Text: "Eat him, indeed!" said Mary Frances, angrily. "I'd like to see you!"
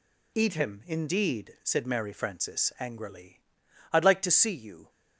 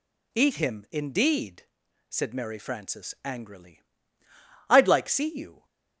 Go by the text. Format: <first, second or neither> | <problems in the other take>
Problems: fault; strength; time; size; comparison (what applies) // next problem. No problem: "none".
first | skips "to"; at 5.0 s